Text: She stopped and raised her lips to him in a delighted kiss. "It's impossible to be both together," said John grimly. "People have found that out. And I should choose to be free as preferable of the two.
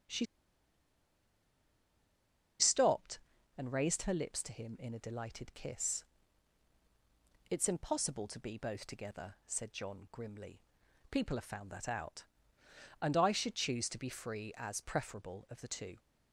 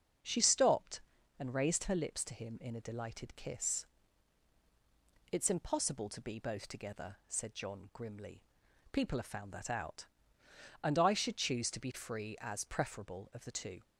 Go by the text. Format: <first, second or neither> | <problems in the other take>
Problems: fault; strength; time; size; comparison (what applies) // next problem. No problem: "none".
second | starts louder than the rest; until 3.8 s; 6.5 dB; also in the second // pauses between "She" and "stopped"; strong; at 0.2 s; 2.3 s long